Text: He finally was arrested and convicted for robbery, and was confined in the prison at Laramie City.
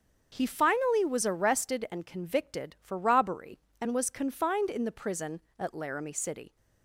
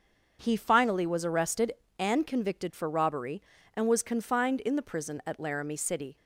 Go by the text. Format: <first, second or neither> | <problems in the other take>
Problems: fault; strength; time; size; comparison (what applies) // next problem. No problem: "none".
neither | starts louder than the rest; the same in both